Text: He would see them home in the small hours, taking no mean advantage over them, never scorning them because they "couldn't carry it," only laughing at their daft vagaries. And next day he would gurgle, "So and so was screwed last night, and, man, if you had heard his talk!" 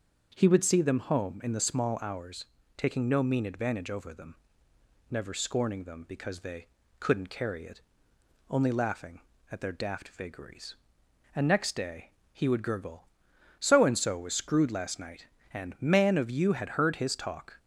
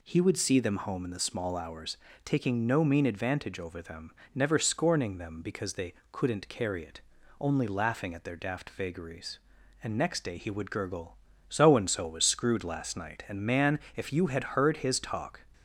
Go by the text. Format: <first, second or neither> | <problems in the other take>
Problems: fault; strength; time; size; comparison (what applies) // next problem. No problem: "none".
second | starts louder than the rest; until 1.3 s; 7 dB // pauses between "they" and "couldn't"; slight; at 6.6 s; 0.30 s long; slight in the second // pauses between "day" and "he"; slight; at 12.1 s; 0.18 s long // says "of" for "if"; at 16.1 s